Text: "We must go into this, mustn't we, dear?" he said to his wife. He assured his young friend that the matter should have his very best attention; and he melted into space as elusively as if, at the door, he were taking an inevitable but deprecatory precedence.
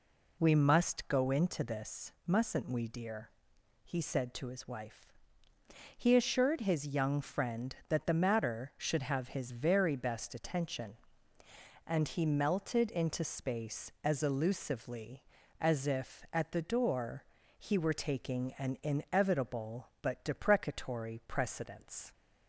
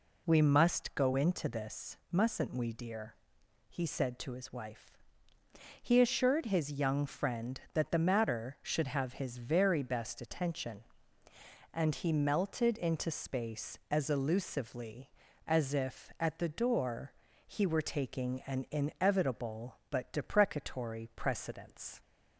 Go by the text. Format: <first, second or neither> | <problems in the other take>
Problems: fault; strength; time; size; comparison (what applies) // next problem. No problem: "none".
neither | none